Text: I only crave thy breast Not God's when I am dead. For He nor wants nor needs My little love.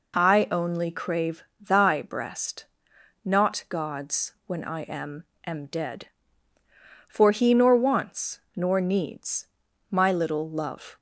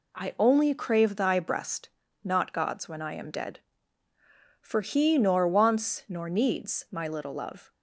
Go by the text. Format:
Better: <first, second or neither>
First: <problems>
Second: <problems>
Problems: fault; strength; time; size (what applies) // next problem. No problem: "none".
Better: second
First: pauses between "crave" and "thy"; slight; at 1.4 s; 0.16 s long // pauses between "breast" and "Not"; noticeable; at 2.6 s; 0.60 s long // pauses between "God's" and "when"; slight; at 4.3 s; 0.16 s long // says "am" twice; at 5.4 s // pauses between "wants" and "nor"; slight; at 8.3 s; 0.16 s long // pauses between "needs" and "My"; at 9.4 s; 0.44 s long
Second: pauses between "breast" and "Not"; slight; at 1.8 s; 0.34 s long